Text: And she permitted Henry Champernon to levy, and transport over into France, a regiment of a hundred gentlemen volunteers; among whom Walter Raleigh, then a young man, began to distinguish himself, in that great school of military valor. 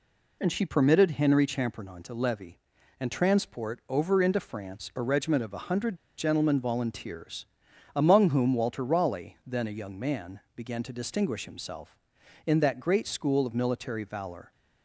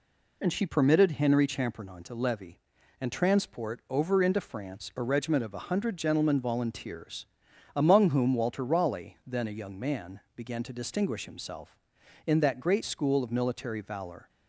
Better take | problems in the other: second | pauses between "hundred" and "gentlemen"; slight; at 5.9 s; 0.20 s long

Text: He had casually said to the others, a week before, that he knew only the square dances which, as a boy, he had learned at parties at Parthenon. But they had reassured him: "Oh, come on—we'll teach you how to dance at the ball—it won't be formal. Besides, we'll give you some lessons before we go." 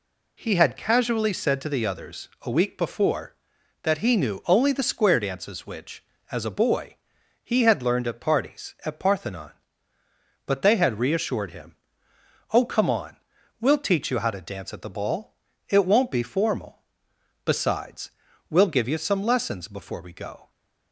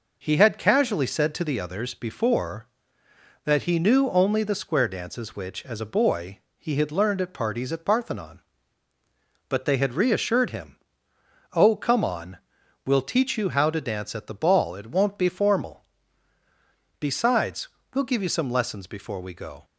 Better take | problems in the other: first | skips "a week"; at 1.9 s

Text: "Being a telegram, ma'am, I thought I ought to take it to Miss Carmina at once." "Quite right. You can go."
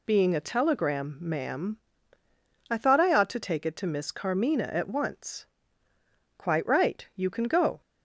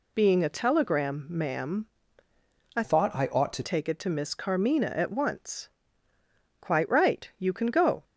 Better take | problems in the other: first | changes voice from "thought" to "to"; from 2.8 to 3.6 s; 0.8 s long

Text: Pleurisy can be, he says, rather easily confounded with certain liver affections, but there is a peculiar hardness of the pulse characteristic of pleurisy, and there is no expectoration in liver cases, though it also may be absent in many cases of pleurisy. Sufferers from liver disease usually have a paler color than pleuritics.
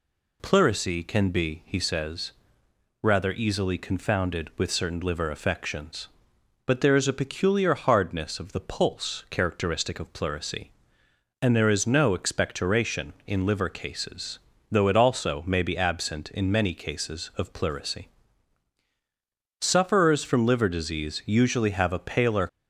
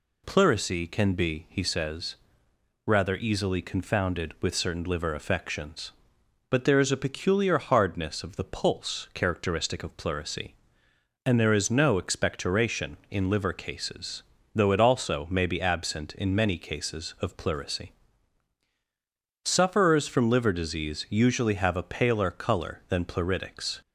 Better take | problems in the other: second | stops before "color than pleuritics"; at 22.4 s

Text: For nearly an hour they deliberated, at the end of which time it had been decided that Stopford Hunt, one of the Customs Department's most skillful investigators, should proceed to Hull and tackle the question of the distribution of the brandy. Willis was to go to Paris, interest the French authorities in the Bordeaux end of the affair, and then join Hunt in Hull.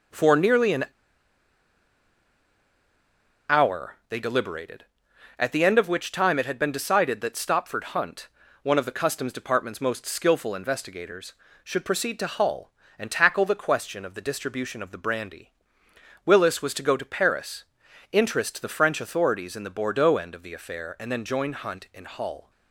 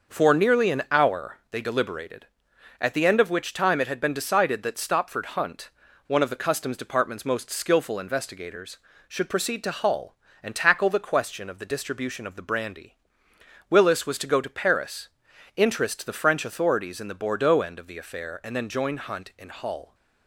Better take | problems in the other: second | starts louder than the rest; noticeable; until 3.7 s; 6 dB; noticeable in the second // pauses between "an" and "hour"; strong; at 0.8 s; 2.6 s long

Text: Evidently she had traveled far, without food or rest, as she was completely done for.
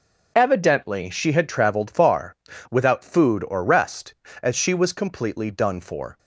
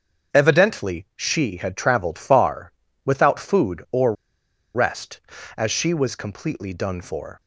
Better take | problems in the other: first | starts louder than the rest; until 1.4 s; 7 dB // pauses between "or" and "rest"; noticeable; at 4.1 s; 0.61 s long

